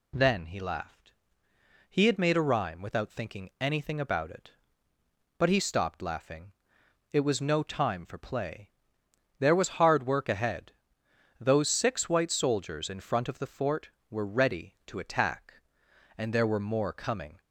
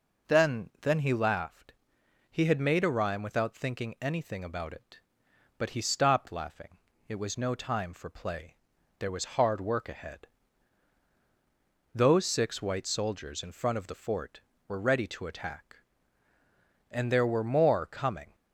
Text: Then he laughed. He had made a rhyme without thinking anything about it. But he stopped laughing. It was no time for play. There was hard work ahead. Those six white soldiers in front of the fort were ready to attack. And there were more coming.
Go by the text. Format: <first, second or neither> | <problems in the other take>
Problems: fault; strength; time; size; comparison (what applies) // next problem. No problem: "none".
first | says "Then" twice; at 0.8 s